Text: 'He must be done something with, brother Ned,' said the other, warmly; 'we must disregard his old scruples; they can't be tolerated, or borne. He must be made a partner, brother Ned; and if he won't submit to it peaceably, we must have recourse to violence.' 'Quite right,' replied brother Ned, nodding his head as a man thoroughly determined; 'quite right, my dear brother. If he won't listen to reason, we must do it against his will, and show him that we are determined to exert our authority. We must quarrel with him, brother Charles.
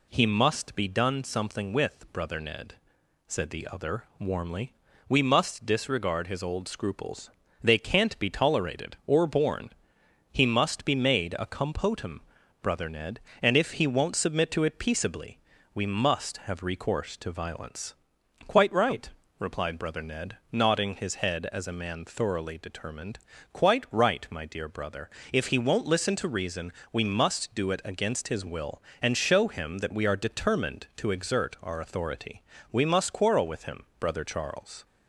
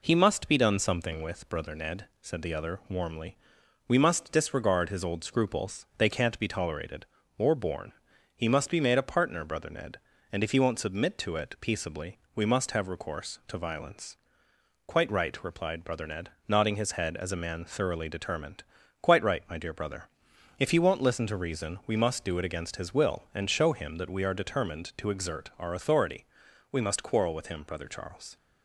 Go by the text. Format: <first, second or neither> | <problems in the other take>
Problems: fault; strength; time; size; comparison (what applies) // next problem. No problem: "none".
second | says "compotum" for "partner"; at 11.4 s